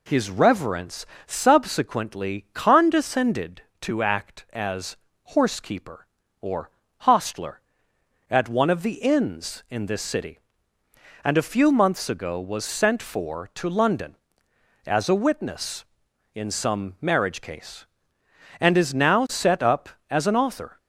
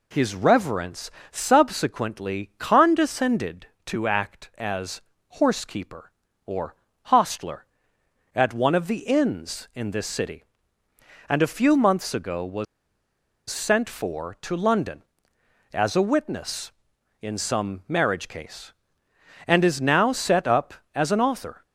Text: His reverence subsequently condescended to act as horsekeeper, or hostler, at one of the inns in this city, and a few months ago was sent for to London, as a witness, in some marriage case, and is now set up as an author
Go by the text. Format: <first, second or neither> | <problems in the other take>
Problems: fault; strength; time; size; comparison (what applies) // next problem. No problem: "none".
first | pauses between "reverence" and "subsequently"; slight; at 1.0 s; 0.22 s long; slight in the first // pauses between "as" and "horsekeeper"; at 4.9 s; 0.40 s long; also in the first // pauses between "or" and "hostler"; slight; at 6.7 s; 0.30 s long; slight in the first // pauses between "was" and "sent"; noticeable; at 12.6 s; 0.84 s long